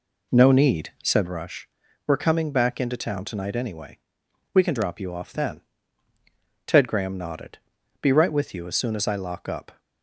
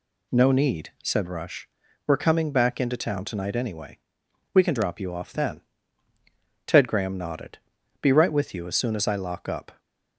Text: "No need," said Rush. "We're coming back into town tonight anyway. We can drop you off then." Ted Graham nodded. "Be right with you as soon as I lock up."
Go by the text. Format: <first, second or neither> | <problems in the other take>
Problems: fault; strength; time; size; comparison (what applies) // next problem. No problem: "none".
second | starts louder than the rest; slight; until 1.4 s; 3 dB